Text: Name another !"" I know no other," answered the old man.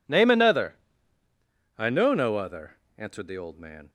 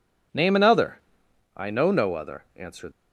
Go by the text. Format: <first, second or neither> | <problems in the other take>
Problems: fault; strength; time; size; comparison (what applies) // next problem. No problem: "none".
first | stops before "the old man"; at 2.9 s